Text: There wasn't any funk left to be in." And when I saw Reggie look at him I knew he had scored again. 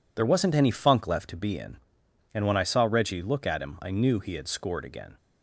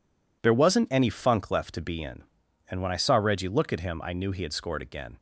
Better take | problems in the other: neither | none

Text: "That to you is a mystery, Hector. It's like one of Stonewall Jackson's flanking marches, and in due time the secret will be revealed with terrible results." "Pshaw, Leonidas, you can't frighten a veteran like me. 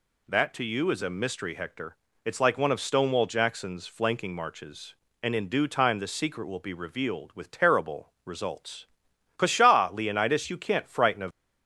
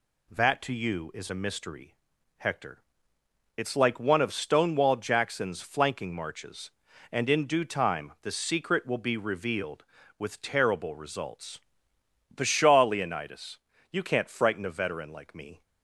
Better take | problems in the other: second | stops before "veteran like me"; at 11.2 s

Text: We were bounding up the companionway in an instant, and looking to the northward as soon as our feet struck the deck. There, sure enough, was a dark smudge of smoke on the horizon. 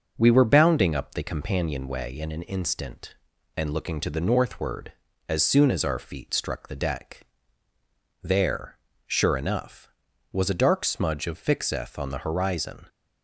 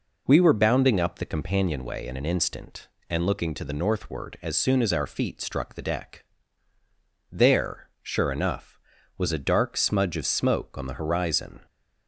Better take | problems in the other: second | says "fixeth" for "smoke"; at 11.3 s

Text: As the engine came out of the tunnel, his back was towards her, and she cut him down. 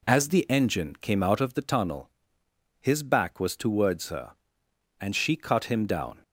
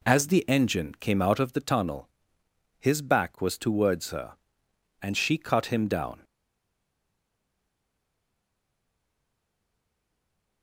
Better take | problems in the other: first | stays silent after the last word; strong; from 6.2 s on; 4.4 s long

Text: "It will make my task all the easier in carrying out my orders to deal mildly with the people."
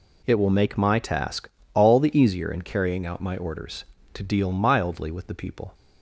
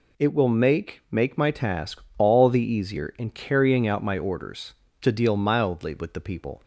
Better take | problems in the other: first | says "make" twice; at 1.1 s // pauses between "task" and "all"; slight; at 2.0 s; 0.18 s long; slight in the first

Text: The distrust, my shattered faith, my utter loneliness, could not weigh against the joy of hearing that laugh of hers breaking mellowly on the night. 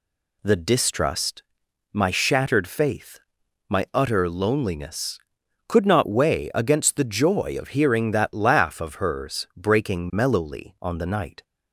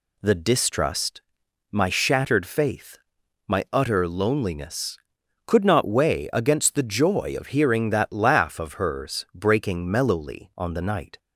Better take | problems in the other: neither | none

